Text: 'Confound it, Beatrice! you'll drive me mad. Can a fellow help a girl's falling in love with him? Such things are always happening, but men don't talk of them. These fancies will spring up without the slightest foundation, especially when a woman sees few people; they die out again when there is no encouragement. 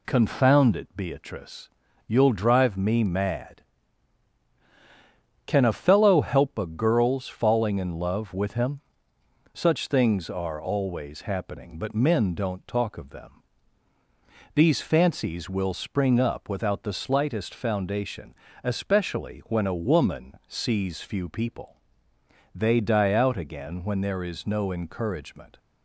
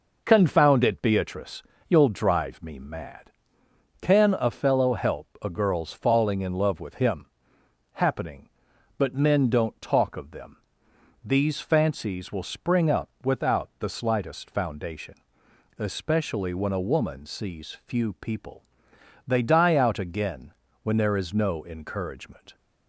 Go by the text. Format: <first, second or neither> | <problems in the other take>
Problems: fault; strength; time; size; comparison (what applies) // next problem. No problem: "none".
first | pauses between "help" and "a"; slight; at 5.2 s; 0.16 s long // skips "Such things are always"; at 7.6 s // pauses between "again" and "when"; slight; at 20.5 s; 0.30 s long